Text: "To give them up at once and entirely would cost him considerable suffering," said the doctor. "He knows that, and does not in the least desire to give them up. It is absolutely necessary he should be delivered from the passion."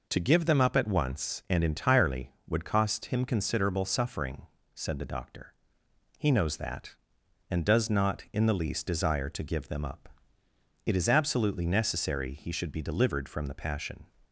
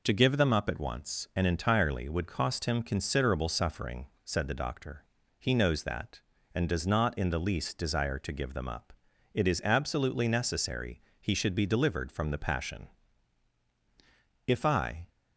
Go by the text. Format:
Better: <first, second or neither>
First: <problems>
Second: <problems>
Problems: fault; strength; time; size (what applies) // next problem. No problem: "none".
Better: first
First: none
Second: pauses between "necessary" and "he"; slight; at 11.0 s; 0.18 s long // goes on to say "If I"; noticeable; from 14.4 s on; 0.62 s long